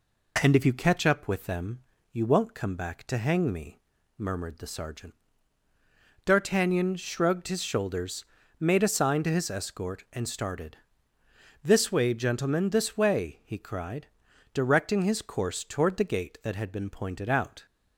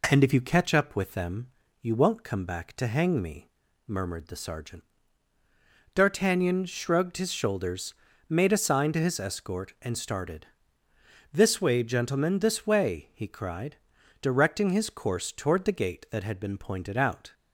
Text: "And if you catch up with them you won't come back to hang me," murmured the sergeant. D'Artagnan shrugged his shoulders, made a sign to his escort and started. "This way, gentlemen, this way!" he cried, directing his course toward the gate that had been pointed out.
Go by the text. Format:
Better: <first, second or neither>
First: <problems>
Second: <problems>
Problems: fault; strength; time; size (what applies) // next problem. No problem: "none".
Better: neither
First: pauses between "them" and "you"; slight; at 1.8 s; 0.30 s long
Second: pauses between "them" and "you"; slight; at 1.4 s; 0.32 s long